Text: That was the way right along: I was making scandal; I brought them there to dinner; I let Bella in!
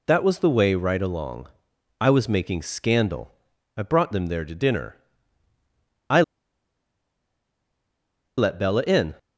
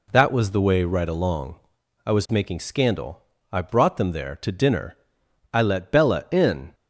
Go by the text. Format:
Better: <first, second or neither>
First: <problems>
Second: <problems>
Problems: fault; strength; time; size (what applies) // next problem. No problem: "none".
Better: second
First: pauses between "I" and "let"; strong; at 6.2 s; 2.1 s long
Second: none